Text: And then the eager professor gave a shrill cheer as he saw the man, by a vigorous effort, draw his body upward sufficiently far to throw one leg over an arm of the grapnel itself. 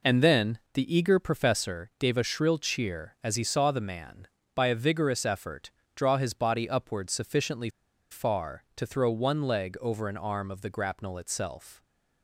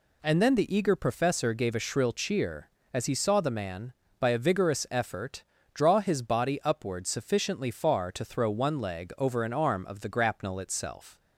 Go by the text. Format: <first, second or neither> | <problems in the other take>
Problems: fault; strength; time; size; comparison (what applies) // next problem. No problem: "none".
second | pauses between "then" and "the"; slight; at 0.5 s; 0.16 s long // pauses between "sufficiently" and "far"; at 7.6 s; 0.42 s long